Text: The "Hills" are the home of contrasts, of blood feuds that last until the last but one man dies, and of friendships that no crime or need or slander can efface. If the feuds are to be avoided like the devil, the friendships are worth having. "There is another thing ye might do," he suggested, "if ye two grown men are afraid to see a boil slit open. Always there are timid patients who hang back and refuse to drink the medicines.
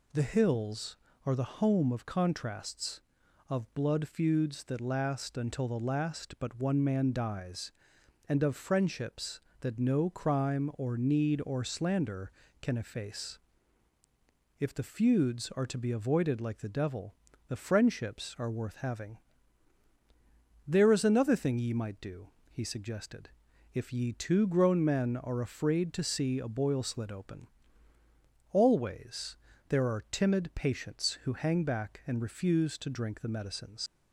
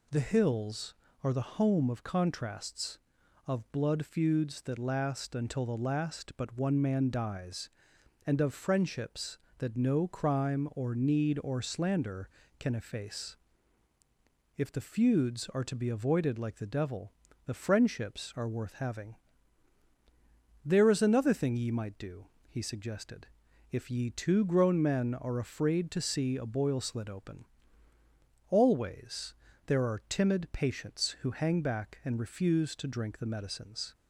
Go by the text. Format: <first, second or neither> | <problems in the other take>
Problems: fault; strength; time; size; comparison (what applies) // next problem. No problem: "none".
second | pauses between "Always" and "there"; slight; at 29.3 s; 0.32 s long; slight in the second // leaves "medicines" unfinished; at 33.8 s; 100 ms